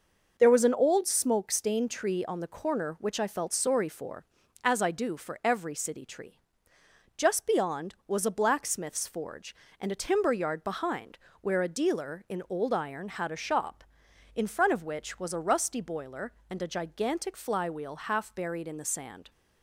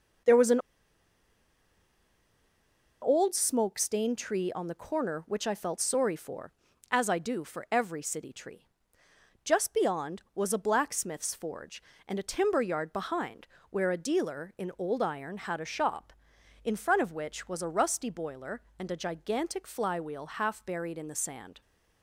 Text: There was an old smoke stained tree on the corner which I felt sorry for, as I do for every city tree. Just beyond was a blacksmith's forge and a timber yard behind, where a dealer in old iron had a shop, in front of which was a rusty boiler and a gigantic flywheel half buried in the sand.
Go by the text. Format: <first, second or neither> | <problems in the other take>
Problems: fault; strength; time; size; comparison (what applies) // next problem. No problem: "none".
first | starts louder than the rest; noticeable; until 3.6 s; 6 dB; noticeable in the first // pauses between "an" and "old"; strong; at 0.5 s; 2.4 s long